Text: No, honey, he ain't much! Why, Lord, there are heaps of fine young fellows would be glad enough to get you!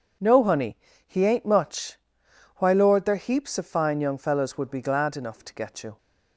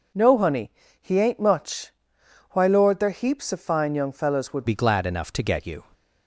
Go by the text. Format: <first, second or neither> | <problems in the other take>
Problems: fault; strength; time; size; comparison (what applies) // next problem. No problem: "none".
first | changes voice at "be"; from 4.6 s on; 1.2 s long